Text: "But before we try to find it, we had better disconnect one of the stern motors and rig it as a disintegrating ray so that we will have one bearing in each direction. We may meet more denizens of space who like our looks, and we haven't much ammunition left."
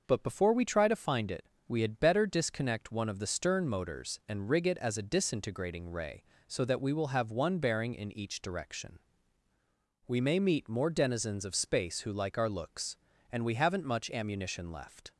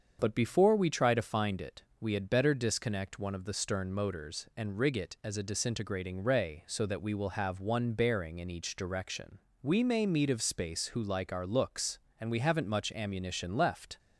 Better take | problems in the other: first | starts louder than the rest; until 1.2 s; 7 dB // skips "more denizens"; at 10.3 s

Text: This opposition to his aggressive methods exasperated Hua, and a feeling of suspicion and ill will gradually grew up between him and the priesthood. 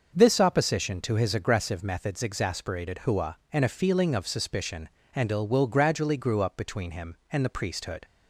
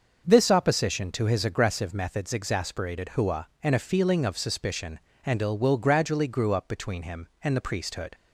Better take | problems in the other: neither | starts louder than the rest; noticeable; the same in both

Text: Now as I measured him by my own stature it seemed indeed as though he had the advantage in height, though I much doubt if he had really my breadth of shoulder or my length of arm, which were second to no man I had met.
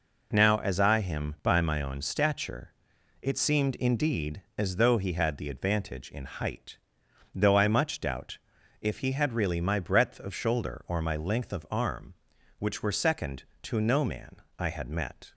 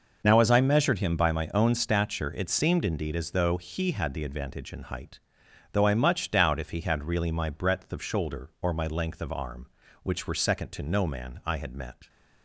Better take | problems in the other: second | skips "measured"; at 1.0 s // pauses between "stature" and "it"; noticeable; at 2.7 s; 0.50 s long // pauses between "doubt" and "if"; at 8.3 s; 0.42 s long // pauses between "man" and "I"; slight; at 14.3 s; 0.22 s long

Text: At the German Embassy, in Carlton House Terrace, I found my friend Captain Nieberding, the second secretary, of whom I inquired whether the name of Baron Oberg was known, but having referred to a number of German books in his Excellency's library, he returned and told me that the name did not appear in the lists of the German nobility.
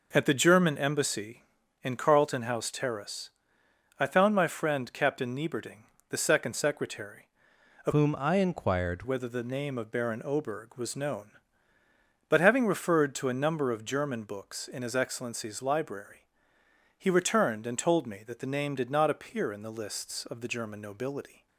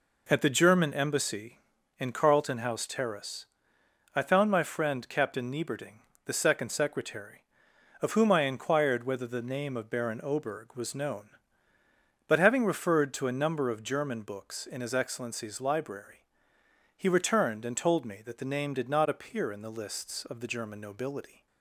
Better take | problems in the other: second | changes voice from "whom" to "inquired"; from 7.9 to 9.0 s; 1.1 s long

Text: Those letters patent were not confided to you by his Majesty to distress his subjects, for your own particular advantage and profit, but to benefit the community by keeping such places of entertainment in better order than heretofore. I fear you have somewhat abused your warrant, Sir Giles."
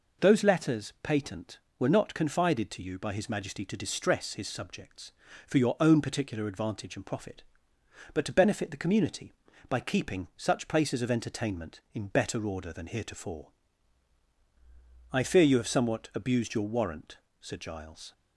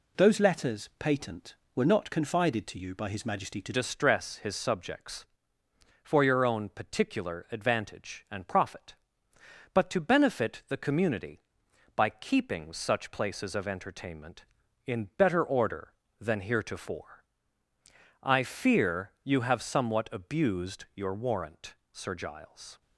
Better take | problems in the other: first | changes voice at "distress"; from 3.7 s on; 19.1 s long

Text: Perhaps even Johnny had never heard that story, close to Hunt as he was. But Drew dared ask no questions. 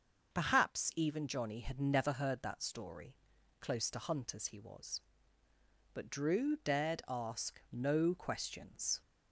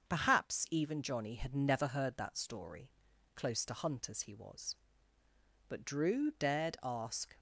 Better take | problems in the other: first | starts louder than the rest; until 1.1 s; 6.5 dB; also in the first // stops before "no questions"; at 7.3 s

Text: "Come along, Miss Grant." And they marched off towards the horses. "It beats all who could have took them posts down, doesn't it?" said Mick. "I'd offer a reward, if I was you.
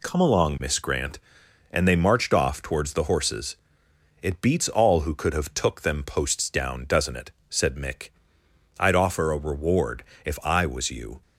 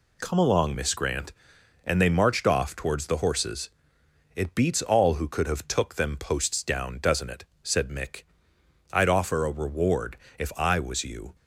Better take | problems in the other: neither | none

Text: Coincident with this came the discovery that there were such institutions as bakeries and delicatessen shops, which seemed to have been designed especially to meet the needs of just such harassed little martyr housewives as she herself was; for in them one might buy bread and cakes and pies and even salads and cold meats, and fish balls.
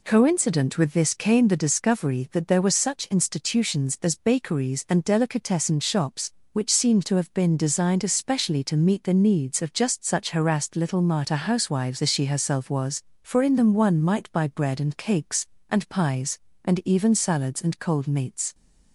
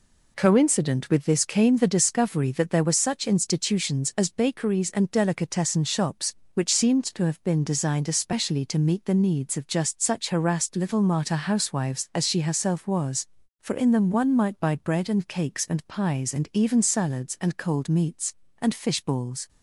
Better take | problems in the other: second | stops before "and fish balls"; at 18.5 s

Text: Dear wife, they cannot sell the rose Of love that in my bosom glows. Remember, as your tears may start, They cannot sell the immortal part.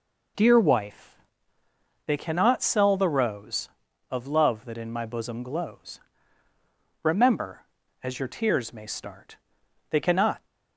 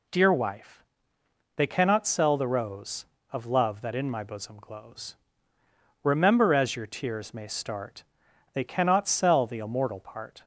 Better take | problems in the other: second | stops before "sell the immortal part"; at 10.4 s

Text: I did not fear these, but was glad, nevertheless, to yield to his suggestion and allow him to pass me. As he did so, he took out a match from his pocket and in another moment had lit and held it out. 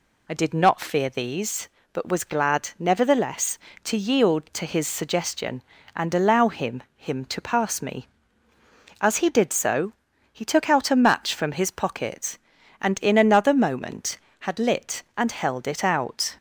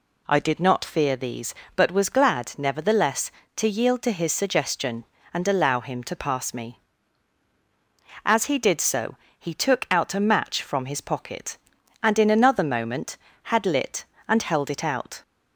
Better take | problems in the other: second | says "him" twice; at 6.9 s

